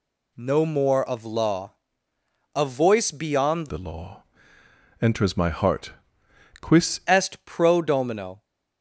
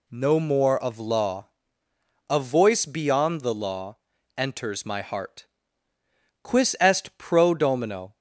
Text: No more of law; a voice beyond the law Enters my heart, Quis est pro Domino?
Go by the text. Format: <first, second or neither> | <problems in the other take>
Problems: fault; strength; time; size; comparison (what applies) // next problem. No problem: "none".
second | changes voice from "the" to "Quis"; from 3.6 to 6.9 s; 3.3 s long // pauses between "law" and "Enters"; noticeable; at 4.2 s; 0.80 s long; also in the second